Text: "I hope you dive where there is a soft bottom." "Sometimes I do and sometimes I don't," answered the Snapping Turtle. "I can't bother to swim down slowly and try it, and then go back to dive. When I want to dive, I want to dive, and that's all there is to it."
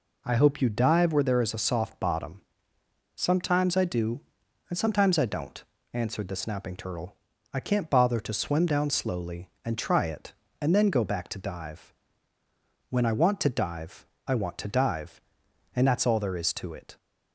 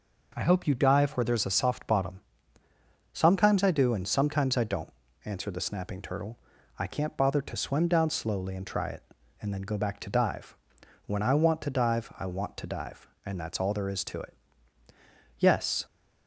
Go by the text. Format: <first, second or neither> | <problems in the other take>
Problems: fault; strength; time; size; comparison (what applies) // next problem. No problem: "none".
first | goes on to say "Yes"; slight; from 15.3 s on; 0.48 s long